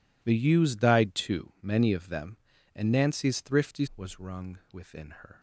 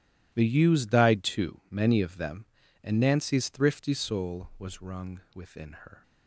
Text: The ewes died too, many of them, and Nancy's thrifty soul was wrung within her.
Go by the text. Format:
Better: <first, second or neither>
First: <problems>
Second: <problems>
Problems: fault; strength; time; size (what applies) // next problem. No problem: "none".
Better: second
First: skips "soul"; at 3.9 s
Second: none